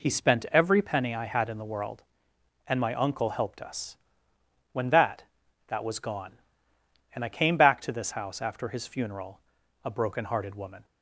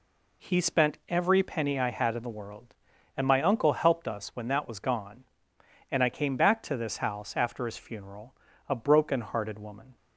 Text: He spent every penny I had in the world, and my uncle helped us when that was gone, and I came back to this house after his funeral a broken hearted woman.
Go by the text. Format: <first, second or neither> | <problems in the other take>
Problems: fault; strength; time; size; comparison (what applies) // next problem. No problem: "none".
second | pauses between "us" and "when"; noticeable; at 3.9 s; 0.76 s long // says "that" twice; at 5.6 s // pauses between "funeral" and "a"; at 9.4 s; 0.44 s long; slight in the second